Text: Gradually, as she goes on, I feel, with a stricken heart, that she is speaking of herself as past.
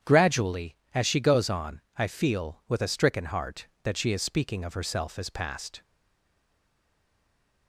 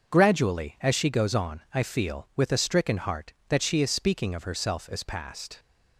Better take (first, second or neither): second